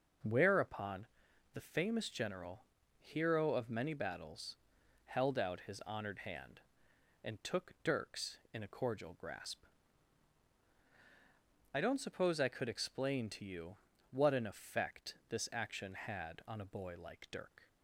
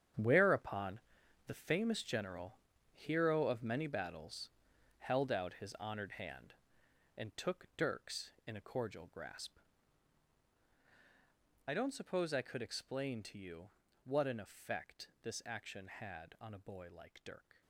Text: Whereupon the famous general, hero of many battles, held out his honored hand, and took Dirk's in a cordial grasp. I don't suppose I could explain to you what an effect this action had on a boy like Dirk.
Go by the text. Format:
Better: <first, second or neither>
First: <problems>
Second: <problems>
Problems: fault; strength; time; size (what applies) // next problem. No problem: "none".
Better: first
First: pauses between "Whereupon" and "the"; noticeable; at 1.0 s; 0.46 s long // pauses between "you" and "what"; slight; at 13.7 s; 0.34 s long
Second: gets quieter; strong; throughout; 12 dB // pauses between "Whereupon" and "the"; noticeable; at 1.0 s; 0.46 s long // pauses between "you" and "what"; slight; at 13.7 s; 0.34 s long